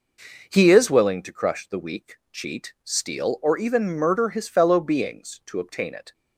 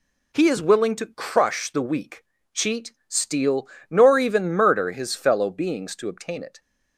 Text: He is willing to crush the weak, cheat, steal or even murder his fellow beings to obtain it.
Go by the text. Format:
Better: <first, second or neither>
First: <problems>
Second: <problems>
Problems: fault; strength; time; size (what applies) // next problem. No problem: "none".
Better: first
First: none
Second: says "nor" for "or"; at 3.8 s